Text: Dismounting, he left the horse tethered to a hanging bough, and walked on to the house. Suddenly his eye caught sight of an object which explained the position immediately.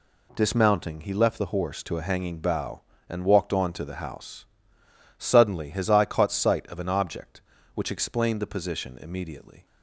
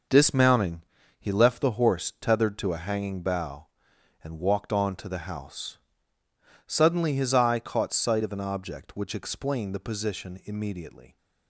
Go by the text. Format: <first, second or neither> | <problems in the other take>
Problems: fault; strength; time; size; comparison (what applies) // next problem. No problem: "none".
second | skips "tethered"; at 1.8 s